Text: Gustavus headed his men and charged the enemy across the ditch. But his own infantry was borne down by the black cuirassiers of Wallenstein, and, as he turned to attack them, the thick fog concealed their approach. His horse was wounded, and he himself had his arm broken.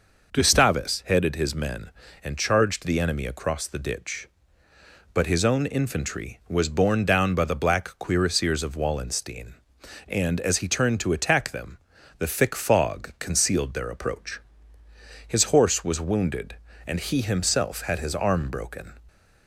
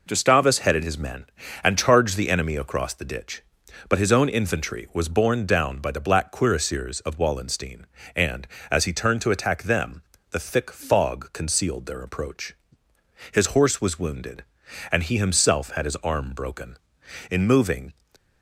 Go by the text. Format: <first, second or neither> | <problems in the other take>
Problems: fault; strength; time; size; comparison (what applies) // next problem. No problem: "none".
first | goes on to say "In moving"; noticeable; from 17.2 s on; 0.64 s long